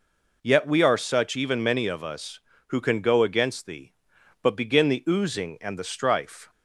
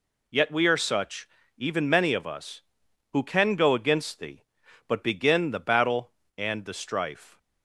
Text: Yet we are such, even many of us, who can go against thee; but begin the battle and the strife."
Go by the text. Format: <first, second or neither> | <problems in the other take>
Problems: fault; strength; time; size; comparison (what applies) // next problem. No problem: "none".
second | says "oozing" for "battle"; at 5.0 s